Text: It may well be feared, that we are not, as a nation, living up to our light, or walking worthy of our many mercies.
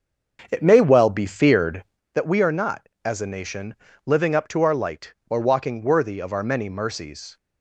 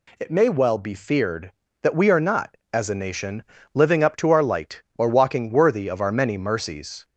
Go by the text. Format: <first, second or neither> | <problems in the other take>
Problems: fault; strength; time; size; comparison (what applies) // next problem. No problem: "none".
second | starts louder than the rest; until 2.0 s; 6.5 dB